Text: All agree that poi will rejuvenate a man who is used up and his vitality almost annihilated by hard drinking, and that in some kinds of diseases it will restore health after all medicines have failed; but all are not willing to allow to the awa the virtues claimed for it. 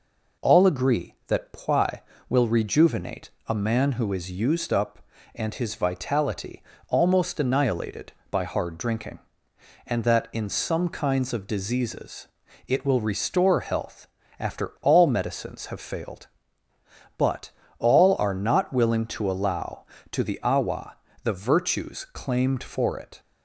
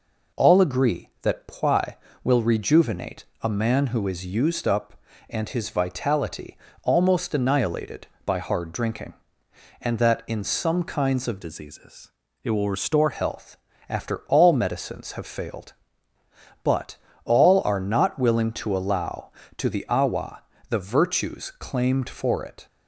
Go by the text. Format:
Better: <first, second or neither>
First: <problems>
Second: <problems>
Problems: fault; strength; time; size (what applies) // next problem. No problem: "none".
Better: first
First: pauses between "rejuvenate" and "a"; slight; at 3.3 s; 0.16 s long // pauses between "vitality" and "almost"; slight; at 6.6 s; 0.26 s long // pauses between "diseases" and "it"; at 12.2 s; 0.40 s long // pauses between "health" and "after"; slight; at 14.0 s; 0.30 s long // pauses between "but" and "all"; slight; at 17.4 s; 0.28 s long // pauses between "awa" and "the"; slight; at 20.9 s; 0.28 s long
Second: pauses between "rejuvenate" and "a"; slight; at 3.2 s; 0.16 s long // pauses between "vitality" and "almost"; slight; at 6.5 s; 0.26 s long // changes voice from "diseases" to "restore"; from 11.4 to 13.1 s; 1.7 s long // pauses between "diseases" and "it"; slight; at 12.1 s; 0.32 s long // pauses between "health" and "after"; slight; at 13.5 s; 0.30 s long // pauses between "but" and "all"; slight; at 16.9 s; 0.28 s long // pauses between "awa" and "the"; slight; at 20.4 s; 0.28 s long